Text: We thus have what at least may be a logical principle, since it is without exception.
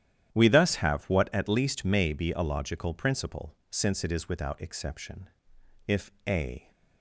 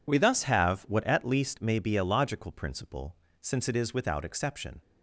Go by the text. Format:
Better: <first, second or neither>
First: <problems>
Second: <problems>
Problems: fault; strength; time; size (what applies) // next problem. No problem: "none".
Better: second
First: starts louder than the rest; strong; until 1.3 s; 11 dB // goes on to say "If a"; noticeable; from 5.8 s on; 0.82 s long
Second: none